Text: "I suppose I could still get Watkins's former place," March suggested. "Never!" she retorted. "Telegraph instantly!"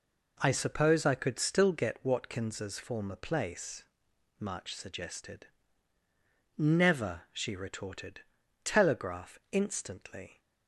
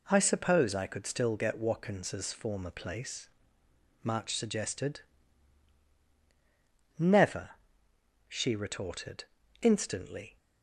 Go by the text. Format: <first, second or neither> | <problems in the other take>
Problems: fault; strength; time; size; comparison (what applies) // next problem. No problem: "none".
first | skips "Telegraph"; at 9.4 s